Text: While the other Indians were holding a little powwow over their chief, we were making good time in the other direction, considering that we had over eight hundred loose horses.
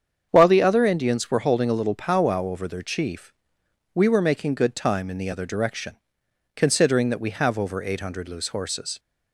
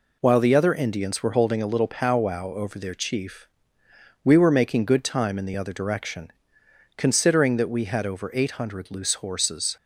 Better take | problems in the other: second | starts louder than the rest; strong; until 1.3 s; 7.5 dB // says "have" for "had"; at 7.2 s

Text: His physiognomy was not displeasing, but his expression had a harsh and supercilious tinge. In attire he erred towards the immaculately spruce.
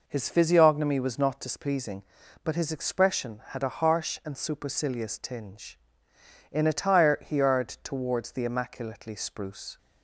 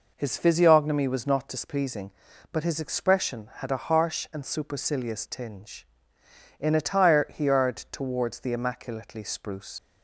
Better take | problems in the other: first | leaves "spruce" unfinished; at 9.7 s; 70 ms

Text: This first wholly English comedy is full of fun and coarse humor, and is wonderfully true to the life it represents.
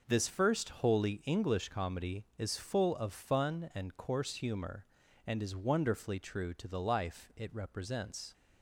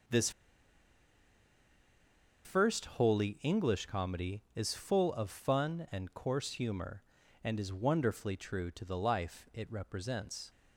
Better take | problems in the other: first | pauses between "This" and "first"; strong; at 0.2 s; 2.1 s long

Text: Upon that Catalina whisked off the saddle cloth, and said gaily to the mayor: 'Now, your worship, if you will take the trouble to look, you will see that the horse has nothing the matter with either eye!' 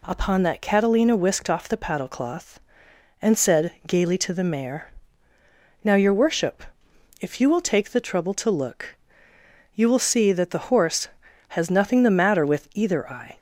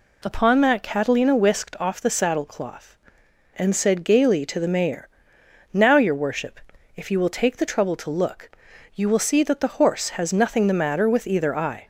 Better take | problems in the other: second | says "paddle" for "saddle"; at 1.7 s // pauses between "said" and "gaily"; slight; at 3.7 s; 0.16 s long

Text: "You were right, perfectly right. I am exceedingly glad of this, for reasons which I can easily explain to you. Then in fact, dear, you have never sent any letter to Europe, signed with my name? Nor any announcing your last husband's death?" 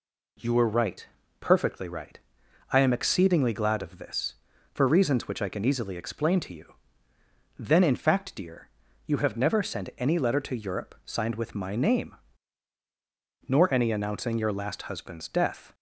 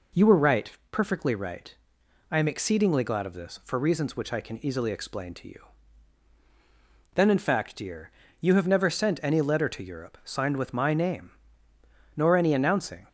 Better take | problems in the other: first | stops before "your last husband's death"; at 13.0 s

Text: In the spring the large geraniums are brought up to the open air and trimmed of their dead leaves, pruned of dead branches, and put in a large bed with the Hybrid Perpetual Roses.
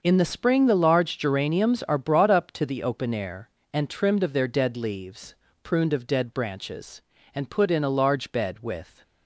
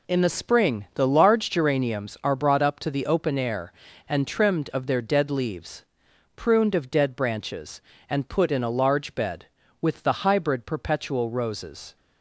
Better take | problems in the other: second | starts louder than the rest; until 1.0 s; 6.5 dB // stops before "the Hybrid Perpetual Roses"; at 9.0 s

